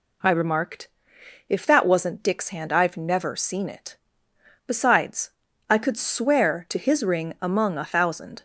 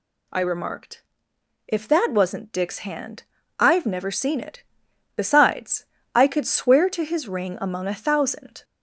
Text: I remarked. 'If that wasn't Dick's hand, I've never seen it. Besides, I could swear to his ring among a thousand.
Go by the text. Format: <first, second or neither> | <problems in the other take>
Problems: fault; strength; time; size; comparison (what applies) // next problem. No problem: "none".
first | gets louder; slight; throughout; 2.5 dB